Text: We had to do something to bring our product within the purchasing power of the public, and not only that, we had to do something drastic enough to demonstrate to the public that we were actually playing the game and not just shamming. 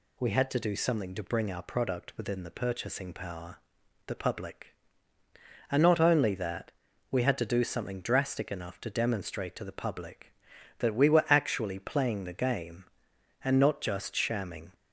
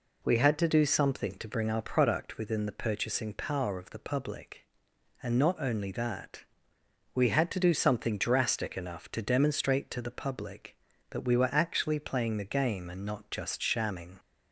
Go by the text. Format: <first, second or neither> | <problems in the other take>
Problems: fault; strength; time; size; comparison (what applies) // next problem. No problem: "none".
second | skips "of"; at 3.8 s